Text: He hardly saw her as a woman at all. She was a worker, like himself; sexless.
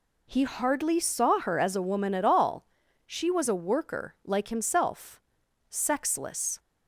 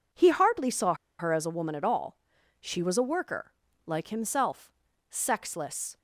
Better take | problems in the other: first | pauses between "saw" and "her"; slight; at 0.9 s; 0.26 s long

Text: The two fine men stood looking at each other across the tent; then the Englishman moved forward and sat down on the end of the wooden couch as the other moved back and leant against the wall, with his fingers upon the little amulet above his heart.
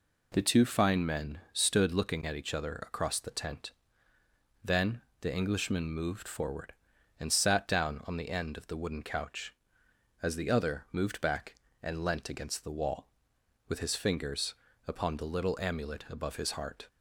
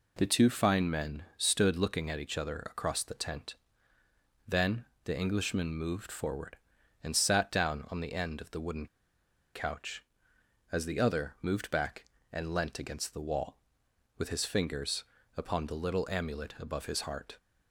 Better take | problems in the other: first | pauses between "then" and "the"; slight; at 4.8 s; 0.18 s long; slight in the first // pauses between "wooden" and "couch"; noticeable; at 8.8 s; 0.67 s long // pauses between "fingers" and "upon"; slight; at 15.0 s; 0.32 s long; slight in the first

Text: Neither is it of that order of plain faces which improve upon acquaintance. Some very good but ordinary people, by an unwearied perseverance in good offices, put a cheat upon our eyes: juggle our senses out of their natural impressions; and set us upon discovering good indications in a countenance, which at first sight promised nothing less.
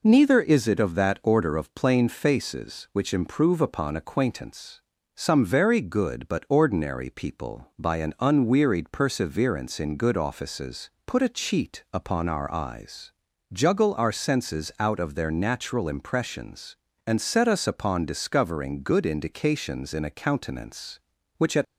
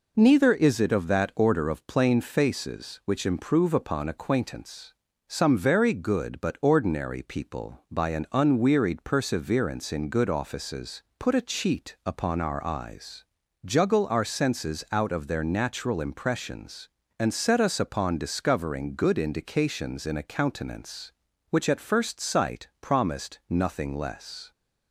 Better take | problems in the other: second | stops before "first sight promised nothing less"; at 21.6 s

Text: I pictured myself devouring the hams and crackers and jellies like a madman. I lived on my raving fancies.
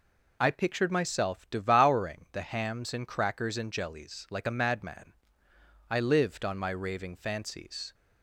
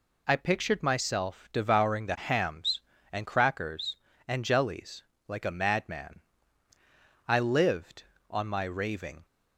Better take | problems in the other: first | pauses between "jellies" and "like"; slight; at 5.0 s; 0.24 s long // stops before "fancies"; at 9.2 s

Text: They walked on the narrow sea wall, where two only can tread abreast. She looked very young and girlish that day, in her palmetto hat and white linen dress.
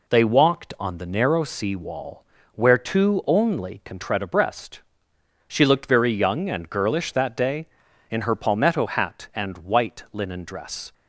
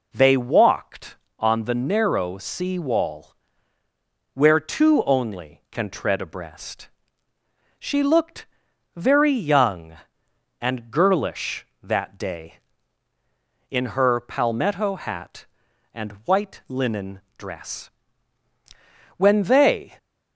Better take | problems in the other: first | pauses between "looked" and "very"; noticeable; at 8.4 s; 0.50 s long // pauses between "linen" and "dress"; slight; at 17.2 s; 0.16 s long // goes on to say "When they"; noticeable; from 19.1 s on; 0.82 s long

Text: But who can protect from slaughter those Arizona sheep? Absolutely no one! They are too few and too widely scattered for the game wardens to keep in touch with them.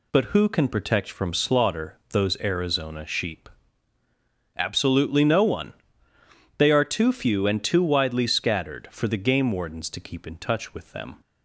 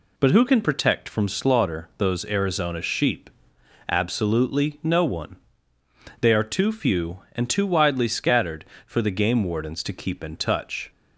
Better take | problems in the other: first | stops before "with them"; at 10.9 s

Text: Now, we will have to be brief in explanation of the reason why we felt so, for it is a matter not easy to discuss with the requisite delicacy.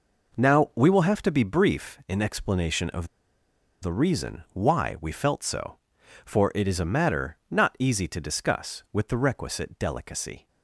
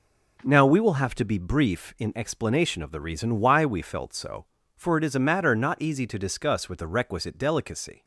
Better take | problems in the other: second | pauses between "of" and "the"; noticeable; at 3.0 s; 0.74 s long

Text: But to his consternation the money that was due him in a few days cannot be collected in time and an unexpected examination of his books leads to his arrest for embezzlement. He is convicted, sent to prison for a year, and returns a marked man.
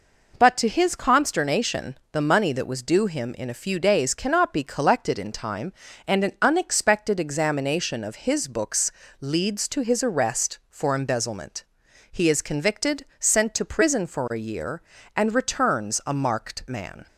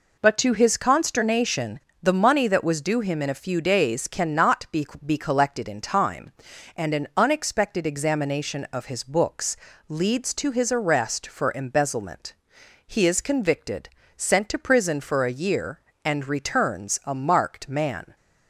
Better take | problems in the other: first | pauses between "consternation" and "the"; slight; at 1.7 s; 0.21 s long; slight in the first // says "be" twice; at 5.0 s // pauses between "books" and "leads"; slight; at 9.5 s; 0.32 s long; slight in the first

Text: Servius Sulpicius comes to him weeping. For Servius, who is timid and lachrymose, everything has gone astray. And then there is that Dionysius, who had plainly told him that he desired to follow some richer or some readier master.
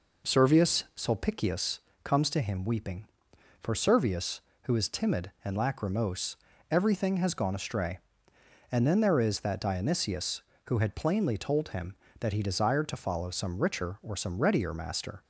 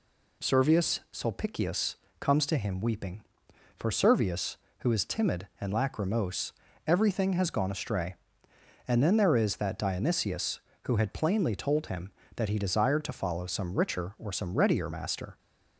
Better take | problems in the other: second | starts louder than the rest; noticeable; until 1.6 s; 4.5 dB // pauses between "Sulpicius" and "comes"; slight; at 1.7 s; 0.26 s long; slight in the second

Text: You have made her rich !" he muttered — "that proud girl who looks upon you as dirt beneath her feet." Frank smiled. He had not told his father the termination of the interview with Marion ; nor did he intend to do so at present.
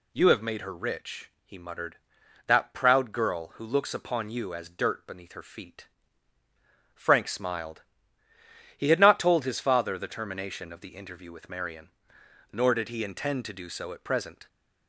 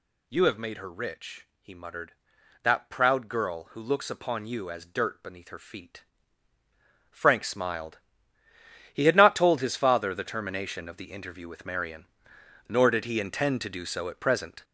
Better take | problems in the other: first | gets louder; throughout; 7 dB

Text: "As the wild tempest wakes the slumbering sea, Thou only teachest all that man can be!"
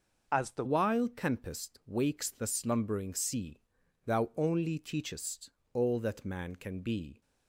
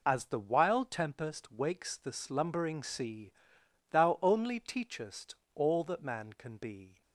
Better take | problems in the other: second | changes voice at "wild"; from 0.6 s on; 6.6 s long // pauses between "teachest" and "all"; slight; at 5.5 s; 0.24 s long; slight in the second

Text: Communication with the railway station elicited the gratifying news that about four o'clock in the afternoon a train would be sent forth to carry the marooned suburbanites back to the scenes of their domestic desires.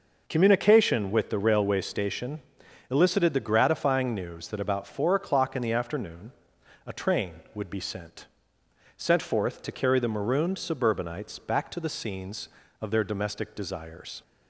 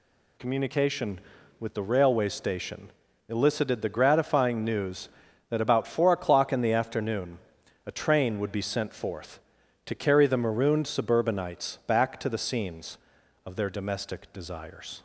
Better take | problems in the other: second | pauses between "station" and "elicited"; noticeable; at 2.4 s; 0.50 s long; also in the second // pauses between "afternoon" and "a"; noticeable; at 6.3 s; 0.54 s long; noticeable in the second // says "sent" twice; at 8.9 s

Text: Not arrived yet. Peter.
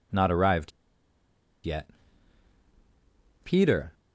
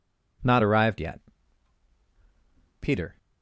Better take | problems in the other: second | pauses between "arrived" and "yet"; noticeable; at 0.7 s; 0.94 s long

